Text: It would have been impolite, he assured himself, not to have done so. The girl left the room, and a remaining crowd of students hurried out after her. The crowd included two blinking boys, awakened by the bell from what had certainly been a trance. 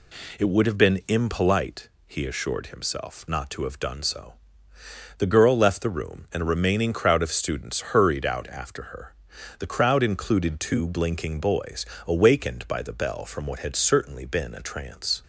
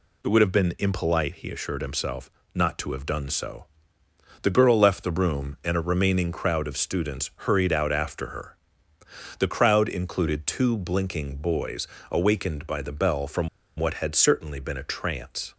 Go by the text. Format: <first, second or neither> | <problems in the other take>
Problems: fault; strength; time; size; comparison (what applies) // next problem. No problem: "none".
first | pauses between "from" and "what"; slight; at 13.4 s; 0.29 s long